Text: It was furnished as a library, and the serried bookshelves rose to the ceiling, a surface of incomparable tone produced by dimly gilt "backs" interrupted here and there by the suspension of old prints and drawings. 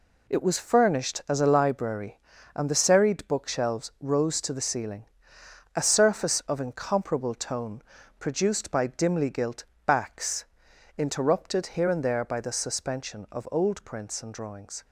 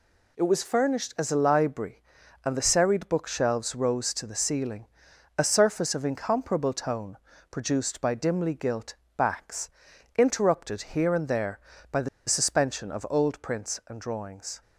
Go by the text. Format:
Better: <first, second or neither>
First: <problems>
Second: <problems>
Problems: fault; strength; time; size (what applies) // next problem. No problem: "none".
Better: first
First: pauses between "tone" and "produced"; slight; at 7.8 s; 0.36 s long // pauses between "gilt" and "backs"; slight; at 9.6 s; 0.20 s long // pauses between "backs" and "interrupted"; noticeable; at 10.4 s; 0.50 s long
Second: pauses between "tone" and "produced"; slight; at 7.1 s; 0.34 s long // pauses between "gilt" and "backs"; slight; at 8.9 s; 0.22 s long // pauses between "backs" and "interrupted"; noticeable; at 9.6 s; 0.48 s long // pauses between "the" and "suspension"; slight; at 12.0 s; 0.19 s long